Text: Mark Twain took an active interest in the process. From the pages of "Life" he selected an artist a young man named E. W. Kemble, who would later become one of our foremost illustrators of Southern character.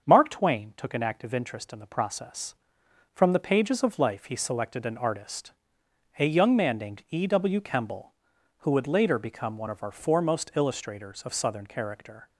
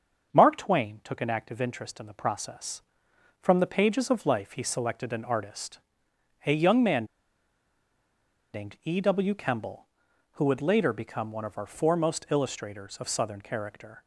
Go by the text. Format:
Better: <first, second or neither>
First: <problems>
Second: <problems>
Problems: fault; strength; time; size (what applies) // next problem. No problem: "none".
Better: first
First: starts louder than the rest; until 1.0 s; 6.5 dB // pauses between "artist" and "a"; noticeable; at 5.5 s; 0.66 s long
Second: starts louder than the rest; until 1.3 s; 6.5 dB // pauses between "artist" and "a"; noticeable; at 5.7 s; 0.66 s long // pauses between "man" and "named"; strong; at 7.0 s; 1.4 s long